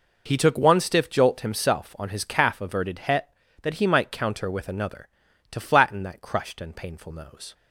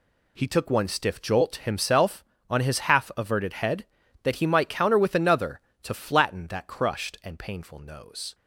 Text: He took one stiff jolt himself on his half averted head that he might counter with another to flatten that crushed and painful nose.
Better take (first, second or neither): second